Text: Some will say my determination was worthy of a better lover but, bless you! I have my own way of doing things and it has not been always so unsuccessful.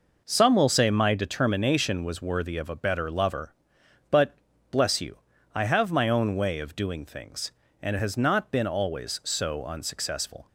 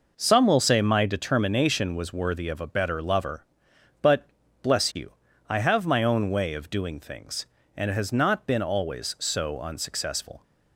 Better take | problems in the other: neither | none

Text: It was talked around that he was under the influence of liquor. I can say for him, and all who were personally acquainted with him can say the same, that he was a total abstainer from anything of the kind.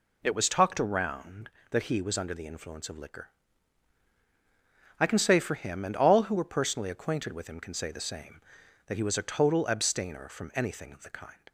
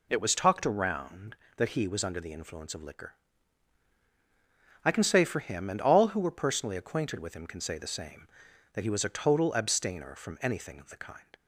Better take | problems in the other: neither | none

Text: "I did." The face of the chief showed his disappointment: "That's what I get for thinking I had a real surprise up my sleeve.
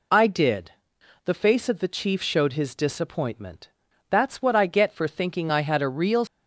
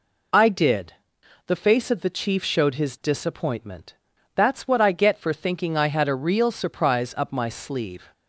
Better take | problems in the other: second | stops before "surprise up my sleeve"; at 6.2 s

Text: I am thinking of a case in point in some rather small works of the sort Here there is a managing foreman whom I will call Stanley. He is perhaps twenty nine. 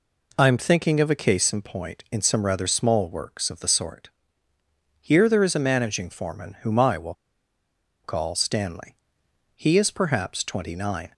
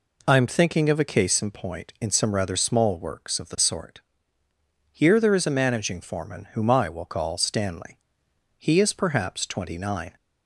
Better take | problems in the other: second | pauses between "sort" and "Here"; noticeable; at 4.0 s; 0.94 s long; noticeable in the second // pauses between "will" and "call"; noticeable; at 7.1 s; 0.91 s long

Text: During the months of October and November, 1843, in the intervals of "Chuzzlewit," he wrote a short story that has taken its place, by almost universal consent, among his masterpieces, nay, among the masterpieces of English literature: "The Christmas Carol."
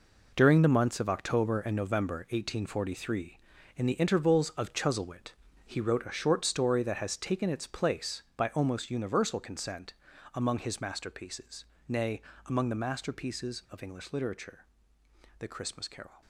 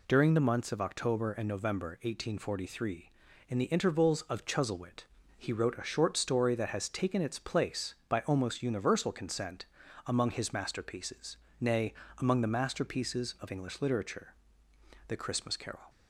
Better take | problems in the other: second | gets quieter; strong; throughout; 11 dB

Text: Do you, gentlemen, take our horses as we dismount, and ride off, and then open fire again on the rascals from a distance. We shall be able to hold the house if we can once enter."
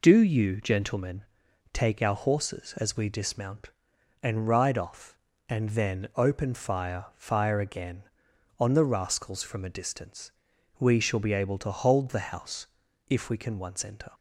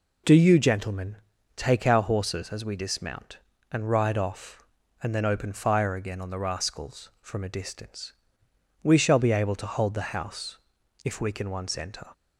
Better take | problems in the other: second | says "fire" twice; at 7.1 s // pauses between "house" and "if"; at 12.6 s; 0.42 s long; also in the second

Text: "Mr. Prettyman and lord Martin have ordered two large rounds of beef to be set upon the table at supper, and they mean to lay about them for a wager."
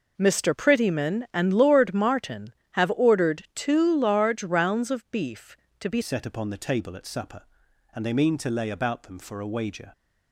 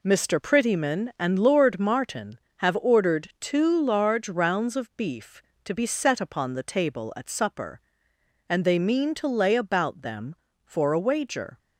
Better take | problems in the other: second | changes voice at "set"; from 6.0 s on; 3.9 s long

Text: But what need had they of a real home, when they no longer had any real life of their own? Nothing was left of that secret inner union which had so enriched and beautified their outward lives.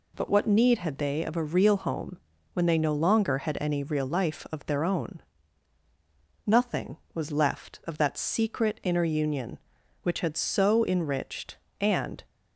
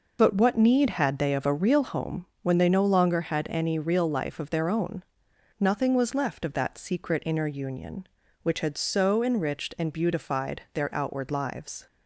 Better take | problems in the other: second | stops before "beautified their outward lives"; at 12.2 s

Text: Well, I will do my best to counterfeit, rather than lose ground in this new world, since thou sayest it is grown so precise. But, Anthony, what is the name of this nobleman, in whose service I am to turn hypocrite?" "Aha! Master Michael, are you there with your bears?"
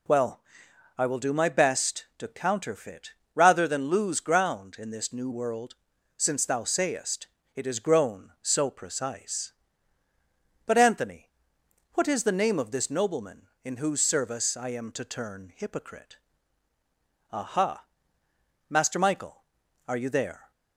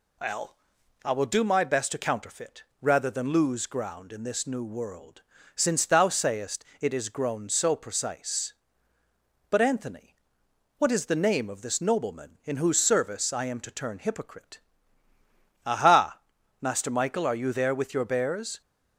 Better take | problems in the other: second | pauses between "sayest" and "it"; slight; at 7.2 s; 0.28 s long; slight in the second // stops before "with your bears"; at 20.5 s

